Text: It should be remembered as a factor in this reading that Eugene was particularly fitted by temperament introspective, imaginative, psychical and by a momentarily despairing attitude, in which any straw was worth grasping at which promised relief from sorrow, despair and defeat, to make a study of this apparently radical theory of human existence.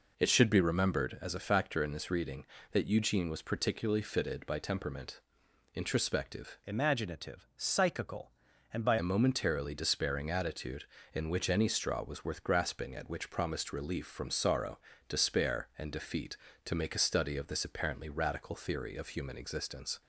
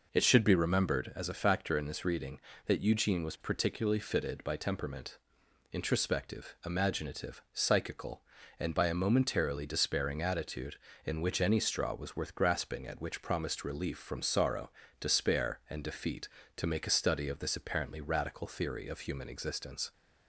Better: second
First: pauses between "temperament" and "introspective"; noticeable; at 5.2 s; 0.54 s long // changes voice from "imaginative" to "by"; from 6.6 to 8.9 s; 2.3 s long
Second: pauses between "temperament" and "introspective"; noticeable; at 5.1 s; 0.54 s long

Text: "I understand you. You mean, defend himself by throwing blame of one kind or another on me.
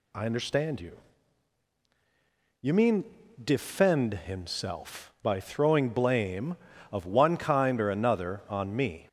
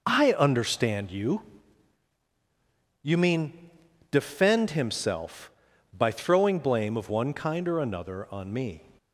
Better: neither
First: none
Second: none

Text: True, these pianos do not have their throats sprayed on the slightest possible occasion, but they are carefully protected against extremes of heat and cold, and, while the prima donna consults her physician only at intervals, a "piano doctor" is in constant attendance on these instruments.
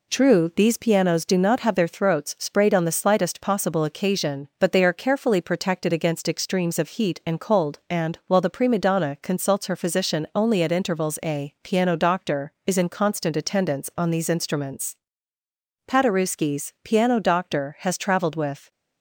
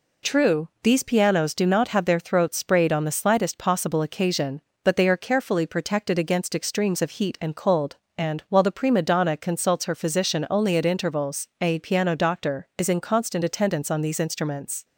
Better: second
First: goes on to say "Paderewski's piano doctor has traveled with"; strong; from 15.8 s on; 2.8 s long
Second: none

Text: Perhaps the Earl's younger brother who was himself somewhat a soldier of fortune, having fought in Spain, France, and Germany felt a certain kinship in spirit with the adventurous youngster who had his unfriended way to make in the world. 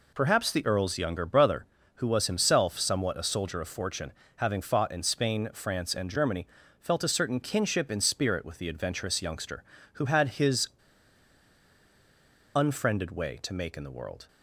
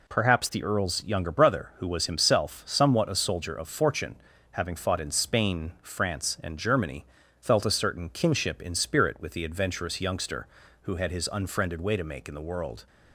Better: second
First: pauses between "Germany" and "felt"; slight; at 6.4 s; 0.32 s long // pauses between "his" and "unfriended"; strong; at 10.6 s; 1.8 s long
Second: pauses between "Germany" and "felt"; slight; at 7.0 s; 0.36 s long

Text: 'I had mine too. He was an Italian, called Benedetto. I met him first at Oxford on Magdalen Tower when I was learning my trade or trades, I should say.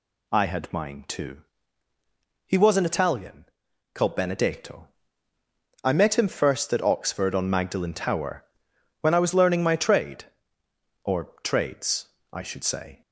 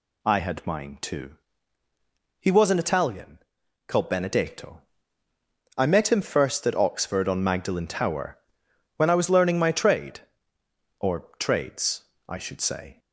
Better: neither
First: pauses between "Tower" and "when"; noticeable; at 8.4 s; 0.58 s long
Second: pauses between "Tower" and "when"; noticeable; at 8.3 s; 0.60 s long

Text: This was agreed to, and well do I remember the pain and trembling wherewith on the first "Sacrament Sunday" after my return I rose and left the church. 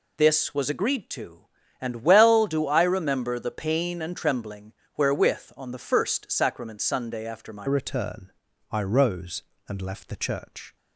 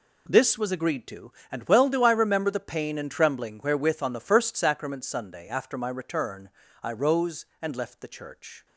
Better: second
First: pauses between "trembling" and "wherewith"; slight; at 4.7 s; 0.22 s long // changes voice at "return"; from 7.6 s on; 3.1 s long // pauses between "return" and "I"; at 8.3 s; 0.38 s long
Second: pauses between "return" and "I"; slight; at 6.4 s; 0.32 s long

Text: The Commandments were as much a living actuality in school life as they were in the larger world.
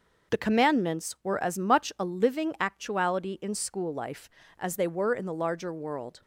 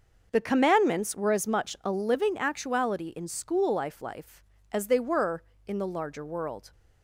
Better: first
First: none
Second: starts louder than the rest; noticeable; until 1.3 s; 6 dB // says "life" twice; at 3.9 s

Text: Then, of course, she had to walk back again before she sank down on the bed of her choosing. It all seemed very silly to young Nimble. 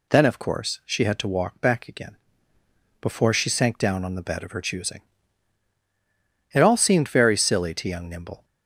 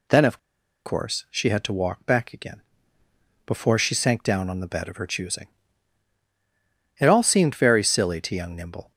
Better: first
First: pauses between "again" and "before"; noticeable; at 2.1 s; 0.84 s long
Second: pauses between "of" and "course"; noticeable; at 0.3 s; 0.48 s long // pauses between "again" and "before"; noticeable; at 2.6 s; 0.84 s long

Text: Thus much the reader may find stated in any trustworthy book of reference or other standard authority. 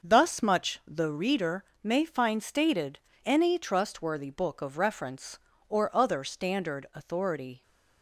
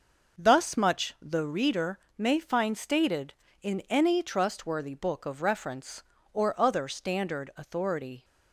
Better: second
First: starts louder than the rest; until 1.1 s; 6.5 dB // pauses between "reader" and "may"; slight; at 1.6 s; 0.18 s long // skips "in"; at 3.1 s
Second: pauses between "reader" and "may"; slight; at 1.9 s; 0.18 s long

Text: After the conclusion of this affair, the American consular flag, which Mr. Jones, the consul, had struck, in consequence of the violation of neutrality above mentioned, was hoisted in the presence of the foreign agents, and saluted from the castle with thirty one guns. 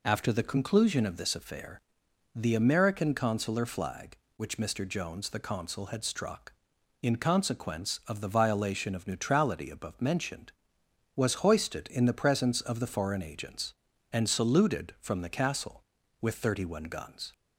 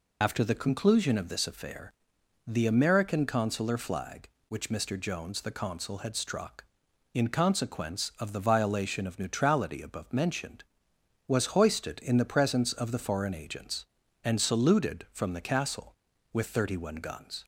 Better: first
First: none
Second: loses the start of "After"; at 0.2 s; 45 ms

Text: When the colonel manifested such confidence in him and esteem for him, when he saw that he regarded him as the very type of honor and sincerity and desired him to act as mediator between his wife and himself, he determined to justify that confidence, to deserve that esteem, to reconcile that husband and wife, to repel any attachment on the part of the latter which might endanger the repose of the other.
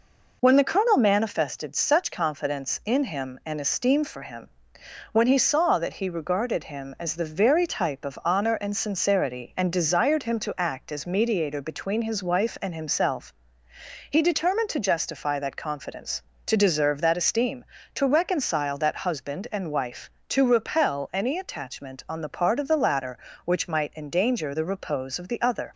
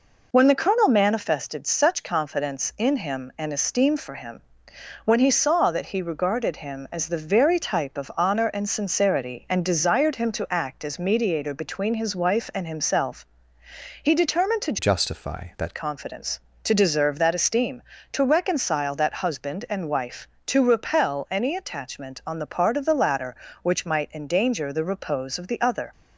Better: first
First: none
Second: changes voice from "justify" to "that"; from 14.7 to 15.7 s; 1.0 s long

